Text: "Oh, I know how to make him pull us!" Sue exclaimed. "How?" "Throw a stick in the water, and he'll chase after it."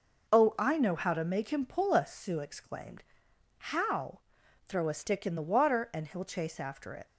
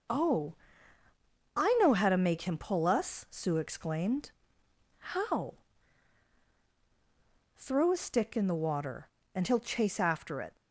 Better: neither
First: none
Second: none

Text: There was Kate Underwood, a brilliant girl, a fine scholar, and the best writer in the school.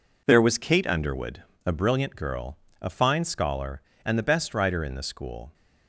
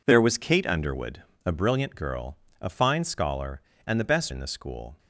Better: first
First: none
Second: skips "writer"; at 4.3 s

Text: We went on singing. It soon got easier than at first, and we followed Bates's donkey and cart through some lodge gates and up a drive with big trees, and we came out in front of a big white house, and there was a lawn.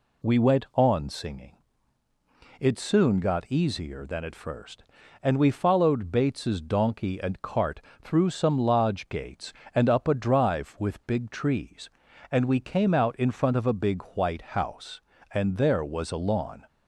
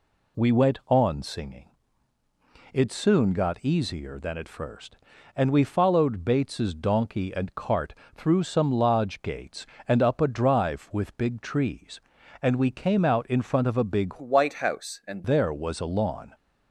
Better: first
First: pauses between "cart" and "through"; slight; at 7.8 s; 0.22 s long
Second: pauses between "cart" and "through"; slight; at 7.9 s; 0.22 s long // changes voice from "white" to "and"; from 14.1 to 15.2 s; 1.1 s long

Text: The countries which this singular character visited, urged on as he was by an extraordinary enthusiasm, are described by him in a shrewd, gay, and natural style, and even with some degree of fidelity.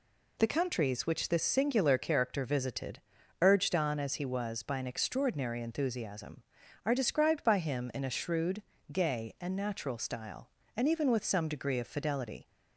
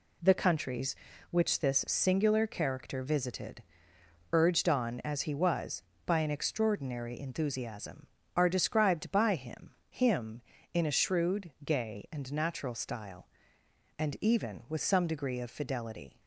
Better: first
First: none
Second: says "him" twice; at 9.9 s

